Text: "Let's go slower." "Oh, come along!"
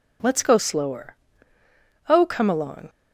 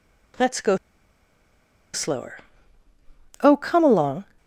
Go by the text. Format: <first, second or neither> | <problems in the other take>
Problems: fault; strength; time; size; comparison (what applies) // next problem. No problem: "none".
first | pauses between "go" and "slower"; at 0.7 s; 1.1 s long